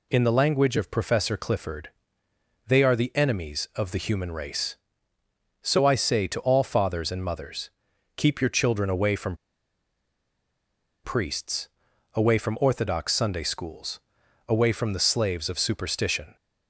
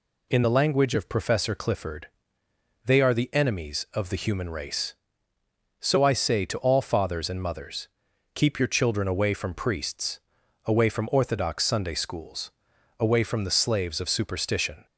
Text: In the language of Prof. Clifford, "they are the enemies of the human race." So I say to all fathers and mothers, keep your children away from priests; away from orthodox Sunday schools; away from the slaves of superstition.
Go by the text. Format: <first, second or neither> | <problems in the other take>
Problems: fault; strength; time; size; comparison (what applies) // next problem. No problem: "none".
second | pauses between "from" and "priests"; strong; at 9.3 s; 1.6 s long